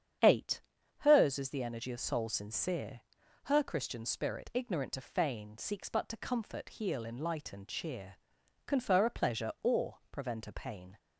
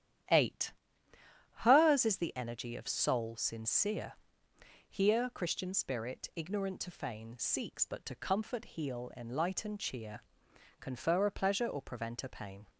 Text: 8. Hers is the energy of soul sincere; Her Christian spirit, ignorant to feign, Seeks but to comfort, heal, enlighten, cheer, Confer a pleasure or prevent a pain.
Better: first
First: starts louder than the rest; strong; until 1.6 s; 8 dB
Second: starts louder than the rest; strong; until 2.2 s; 10.5 dB // says "Here" for "Her"; at 4.8 s

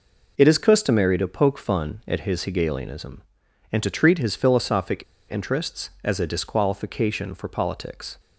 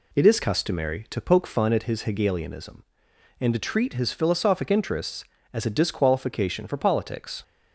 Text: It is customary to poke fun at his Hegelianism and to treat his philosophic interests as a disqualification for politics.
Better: second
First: pauses between "philosophic" and "interests"; slight; at 5.0 s; 0.27 s long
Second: none

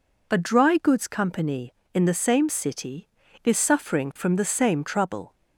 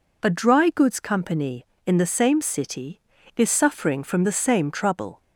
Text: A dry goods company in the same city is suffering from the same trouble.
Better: neither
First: none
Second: none

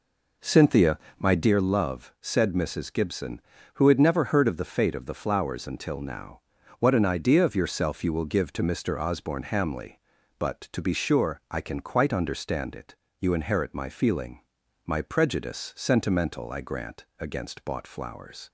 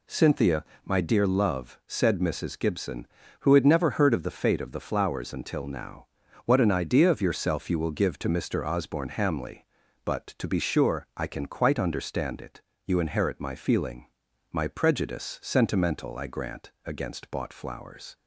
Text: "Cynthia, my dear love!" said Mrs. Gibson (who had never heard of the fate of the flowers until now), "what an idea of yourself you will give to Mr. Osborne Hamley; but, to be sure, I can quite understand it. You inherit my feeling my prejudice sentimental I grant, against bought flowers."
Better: second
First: starts louder than the rest; noticeable; until 1.6 s; 4 dB // pauses between "feeling" and "my"; noticeable; at 14.3 s; 0.46 s long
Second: pauses between "feeling" and "my"; noticeable; at 14.0 s; 0.46 s long

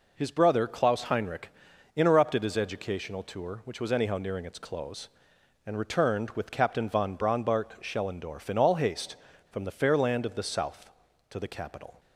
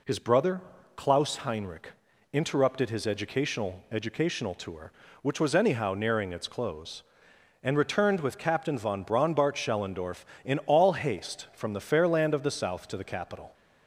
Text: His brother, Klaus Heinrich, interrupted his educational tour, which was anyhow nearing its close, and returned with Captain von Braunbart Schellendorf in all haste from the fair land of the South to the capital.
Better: first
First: none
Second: says "educational" twice; at 3.9 s

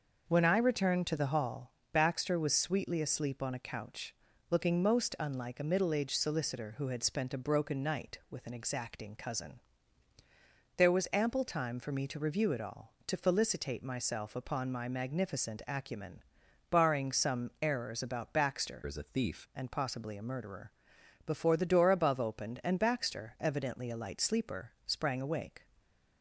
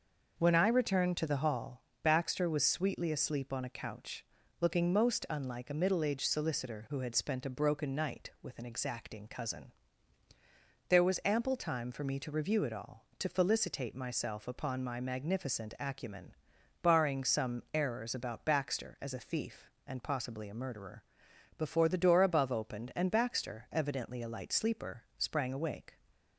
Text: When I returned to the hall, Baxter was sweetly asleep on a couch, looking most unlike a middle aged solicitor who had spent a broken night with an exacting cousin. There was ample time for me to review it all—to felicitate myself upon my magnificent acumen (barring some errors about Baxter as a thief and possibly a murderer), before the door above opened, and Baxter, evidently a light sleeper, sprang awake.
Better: second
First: starts louder than the rest; noticeable; until 1.2 s; 6 dB // changes voice from "as" to "thief"; from 18.8 to 19.4 s; 0.6 s long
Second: starts louder than the rest; noticeable; until 1.4 s; 6 dB

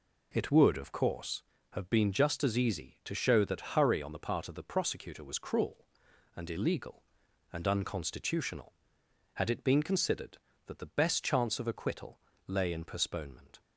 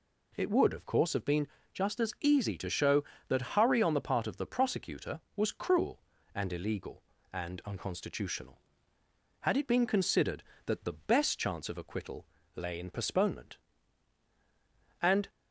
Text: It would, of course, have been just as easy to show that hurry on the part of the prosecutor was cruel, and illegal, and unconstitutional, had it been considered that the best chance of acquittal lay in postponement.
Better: first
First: pauses between "acquittal" and "lay"; slight; at 12.1 s; 0.28 s long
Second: pauses between "been" and "just"; slight; at 1.4 s; 0.26 s long // pauses between "acquittal" and "lay"; slight; at 12.2 s; 0.30 s long // goes on to say "And"; slight; from 15.0 s on; 0.28 s long

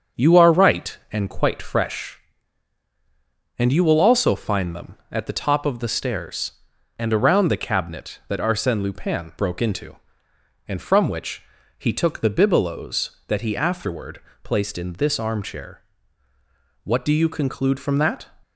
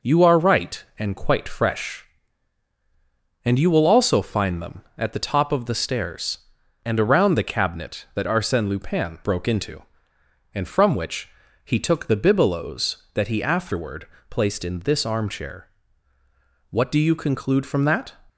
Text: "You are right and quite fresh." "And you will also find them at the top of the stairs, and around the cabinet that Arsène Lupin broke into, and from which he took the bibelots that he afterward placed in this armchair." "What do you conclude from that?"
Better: second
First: starts louder than the rest; until 1.5 s; 6.5 dB // pauses between "which" and "he"; slight; at 11.4 s; 0.36 s long // pauses between "afterward" and "placed"; slight; at 14.2 s; 0.24 s long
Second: pauses between "which" and "he"; slight; at 11.2 s; 0.36 s long // pauses between "afterward" and "placed"; slight; at 14.0 s; 0.24 s long

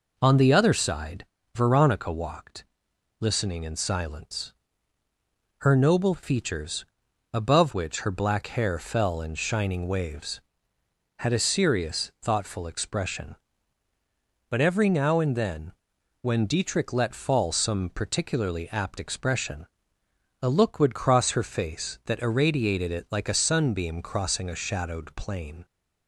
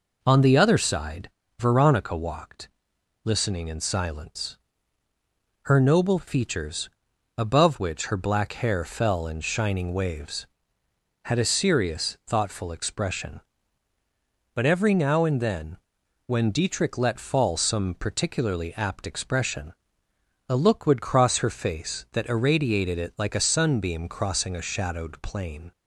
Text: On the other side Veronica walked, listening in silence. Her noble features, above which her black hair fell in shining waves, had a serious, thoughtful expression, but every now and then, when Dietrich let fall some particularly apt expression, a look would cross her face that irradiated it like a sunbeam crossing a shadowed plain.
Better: neither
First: pauses between "side" and "Veronica"; slight; at 1.2 s; 0.30 s long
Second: pauses between "side" and "Veronica"; slight; at 1.2 s; 0.30 s long

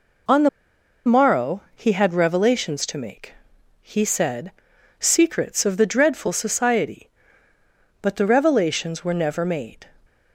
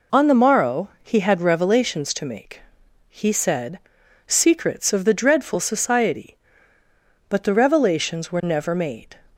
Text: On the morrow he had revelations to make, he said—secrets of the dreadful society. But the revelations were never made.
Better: second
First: pauses between "the" and "morrow"; noticeable; at 0.4 s; 0.57 s long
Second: none

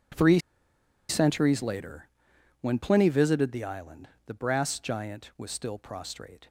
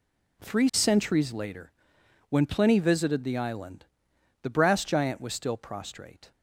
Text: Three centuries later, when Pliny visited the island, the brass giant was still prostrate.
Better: second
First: pauses between "Three" and "centuries"; noticeable; at 0.3 s; 0.70 s long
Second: none

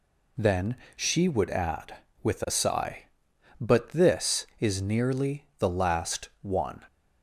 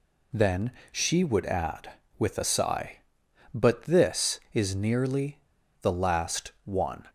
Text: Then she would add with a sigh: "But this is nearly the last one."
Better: first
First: pauses between "Then" and "she"; slight; at 0.7 s; 0.20 s long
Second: pauses between "Then" and "she"; slight; at 0.7 s; 0.20 s long // pauses between "nearly" and "the"; at 5.3 s; 0.43 s long

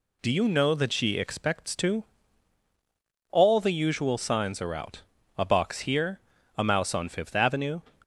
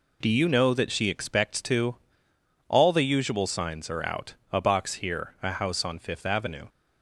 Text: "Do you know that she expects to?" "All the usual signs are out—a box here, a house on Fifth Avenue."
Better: second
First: says "mouse" for "house"; at 6.6 s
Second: none

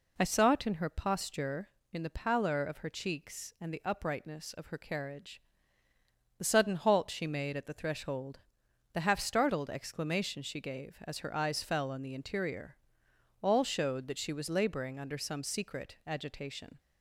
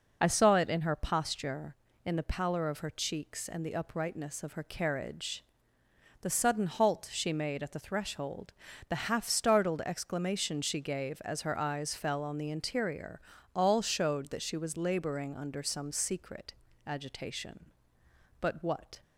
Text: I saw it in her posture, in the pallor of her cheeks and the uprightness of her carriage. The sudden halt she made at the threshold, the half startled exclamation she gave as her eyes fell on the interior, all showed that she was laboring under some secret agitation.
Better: first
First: none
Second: pauses between "secret" and "agitation"; slight; at 16.5 s; 0.32 s long // goes on to say "But what"; noticeable; from 18.3 s on; 0.62 s long

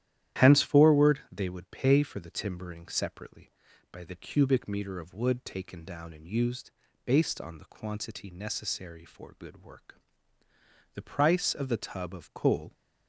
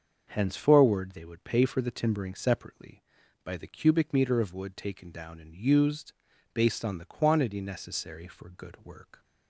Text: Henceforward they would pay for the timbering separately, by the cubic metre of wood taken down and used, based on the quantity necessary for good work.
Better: second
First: starts louder than the rest; strong; until 1.4 s; 12 dB // goes on to say "The price of the tub of coal"; strong; from 10.9 s on; 1.8 s long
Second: starts louder than the rest; until 1.2 s; 6.5 dB

